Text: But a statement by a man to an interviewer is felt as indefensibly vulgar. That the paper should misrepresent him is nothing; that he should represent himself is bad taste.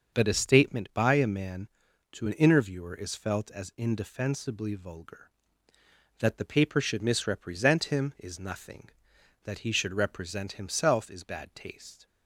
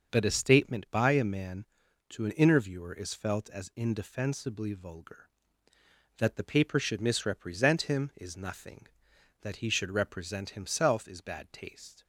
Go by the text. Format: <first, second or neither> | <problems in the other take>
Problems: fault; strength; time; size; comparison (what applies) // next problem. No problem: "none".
neither | starts louder than the rest; the same in both